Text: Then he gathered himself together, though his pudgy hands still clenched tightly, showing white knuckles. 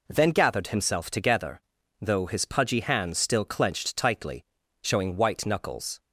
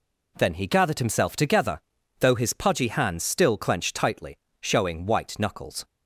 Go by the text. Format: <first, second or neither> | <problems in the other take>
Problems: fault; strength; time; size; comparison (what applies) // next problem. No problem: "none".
second | skips "he"; at 0.3 s